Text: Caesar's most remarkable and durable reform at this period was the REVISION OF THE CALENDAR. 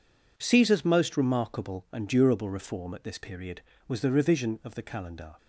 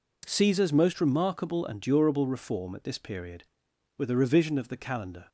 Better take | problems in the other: first | says "were" for "was"; at 3.9 s

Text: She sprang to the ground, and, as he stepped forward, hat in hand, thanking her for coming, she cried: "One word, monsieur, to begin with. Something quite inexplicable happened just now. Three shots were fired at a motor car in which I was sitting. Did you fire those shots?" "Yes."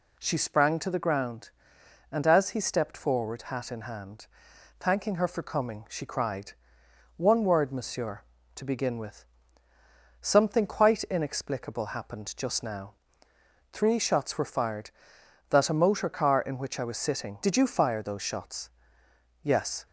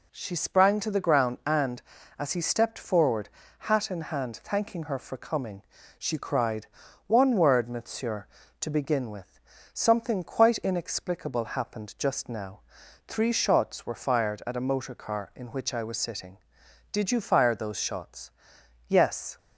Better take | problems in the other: second | says "that" for "at"; at 15.4 s

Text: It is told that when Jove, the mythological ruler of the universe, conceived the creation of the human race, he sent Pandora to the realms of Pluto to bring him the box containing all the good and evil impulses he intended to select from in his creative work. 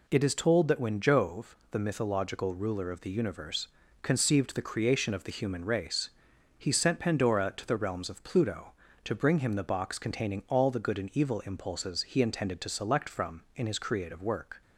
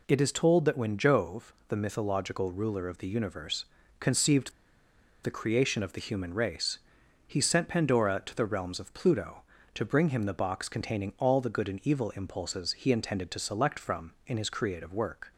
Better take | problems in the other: first | pauses between "conceived" and "the"; noticeable; at 4.5 s; 0.72 s long

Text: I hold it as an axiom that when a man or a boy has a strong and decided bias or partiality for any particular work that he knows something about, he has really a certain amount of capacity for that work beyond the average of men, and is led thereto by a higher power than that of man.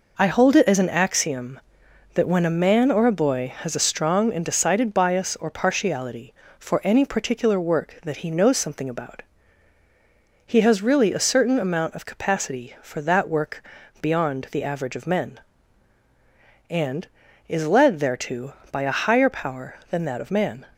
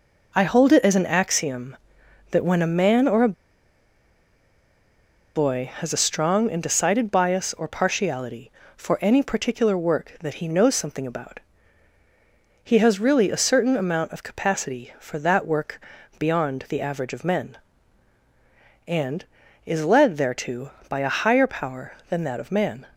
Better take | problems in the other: first | pauses between "a" and "boy"; strong; at 3.3 s; 2.0 s long // pauses between "work" and "beyond"; at 15.7 s; 0.40 s long; also in the first

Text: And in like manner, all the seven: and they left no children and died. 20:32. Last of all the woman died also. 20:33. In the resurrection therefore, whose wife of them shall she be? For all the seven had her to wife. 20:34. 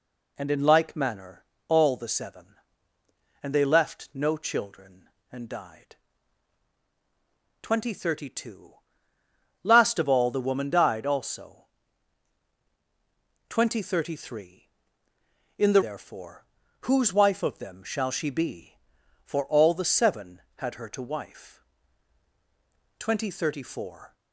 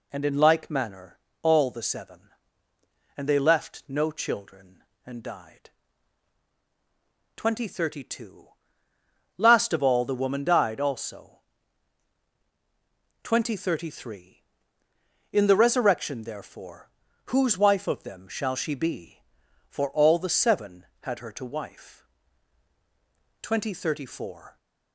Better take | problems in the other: second | skips "resurrection"; at 15.8 s

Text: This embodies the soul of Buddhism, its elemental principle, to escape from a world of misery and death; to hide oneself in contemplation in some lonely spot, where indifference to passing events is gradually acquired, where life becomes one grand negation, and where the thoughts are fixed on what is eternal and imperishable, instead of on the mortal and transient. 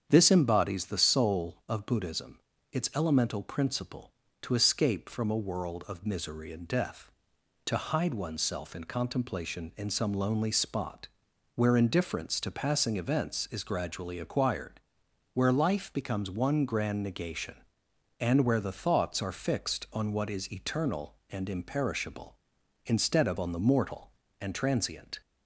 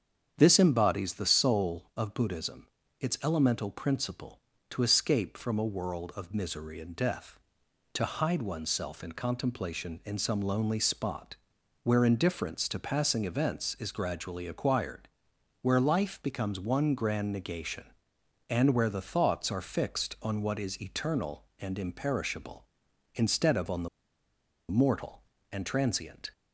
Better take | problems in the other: first | starts louder than the rest; strong; until 1.3 s; 8 dB; strong in the first // pauses between "the" and "mortal"; noticeable; at 23.8 s; 0.81 s long

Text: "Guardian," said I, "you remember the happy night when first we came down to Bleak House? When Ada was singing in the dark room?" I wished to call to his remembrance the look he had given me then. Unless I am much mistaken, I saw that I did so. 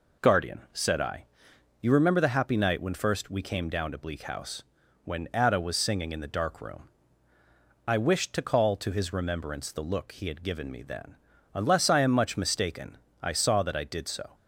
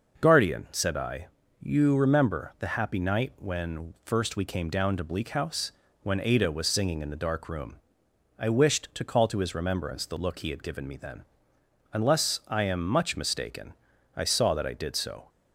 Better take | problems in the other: neither | none

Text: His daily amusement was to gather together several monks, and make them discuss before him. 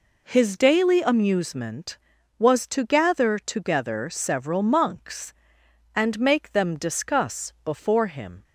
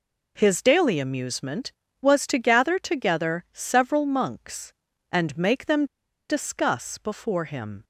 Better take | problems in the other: first | pauses between "them" and "discuss"; at 5.8 s; 0.42 s long

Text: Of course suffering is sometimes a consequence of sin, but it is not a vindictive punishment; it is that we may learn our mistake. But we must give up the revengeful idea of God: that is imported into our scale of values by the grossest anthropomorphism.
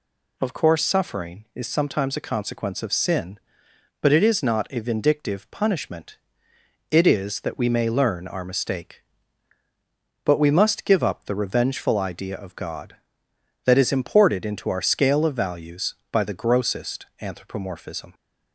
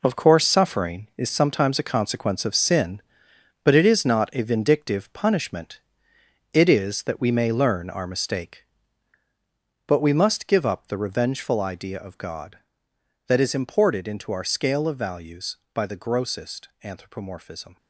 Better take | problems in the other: first | gets quieter; strong; throughout; 9.5 dB

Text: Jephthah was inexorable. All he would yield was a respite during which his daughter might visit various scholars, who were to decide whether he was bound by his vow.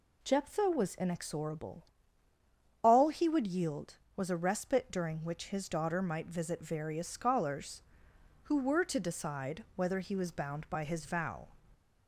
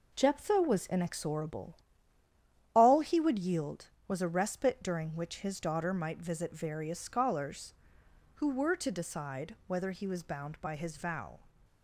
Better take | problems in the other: first | gets quieter; throughout; 6 dB

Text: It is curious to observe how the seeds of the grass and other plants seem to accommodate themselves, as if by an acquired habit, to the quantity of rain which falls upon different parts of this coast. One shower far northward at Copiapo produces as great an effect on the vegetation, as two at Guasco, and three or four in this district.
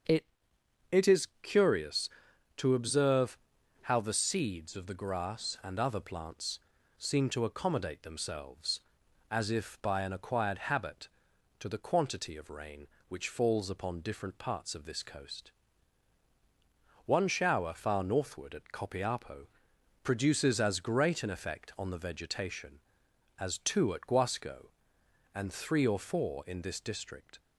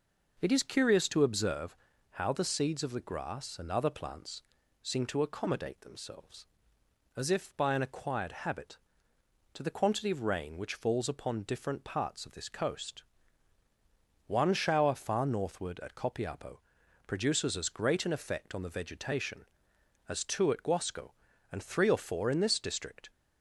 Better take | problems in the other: second | starts louder than the rest; until 1.8 s; 6.5 dB // says "It" twice; at 0.9 s // pauses between "observe" and "how"; noticeable; at 3.3 s; 0.46 s long; slight in the second // pauses between "plants" and "seem"; at 6.5 s; 0.40 s long; also in the second // pauses between "Copiapo" and "produces"; noticeable; at 19.4 s; 0.56 s long; noticeable in the second

